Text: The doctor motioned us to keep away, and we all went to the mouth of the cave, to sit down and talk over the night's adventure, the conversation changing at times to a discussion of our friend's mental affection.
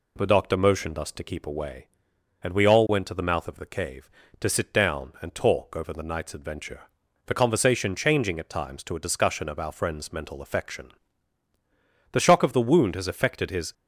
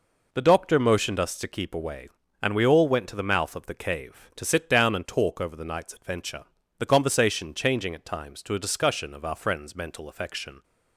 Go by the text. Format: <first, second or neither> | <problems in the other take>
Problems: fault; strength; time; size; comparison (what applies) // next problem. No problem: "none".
second | goes on to say "The shock of the wound has affected his"; from 12.1 s on; 1.6 s long